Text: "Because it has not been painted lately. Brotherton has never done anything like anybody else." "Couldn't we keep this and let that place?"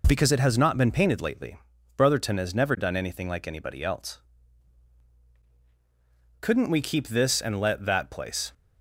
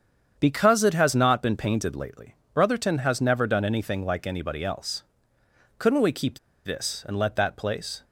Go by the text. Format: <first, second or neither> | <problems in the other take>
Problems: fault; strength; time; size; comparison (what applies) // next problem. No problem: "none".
first | starts louder than the rest; strong; until 1.4 s; 8 dB // pauses between "keep" and "this"; slight; at 6.3 s; 0.26 s long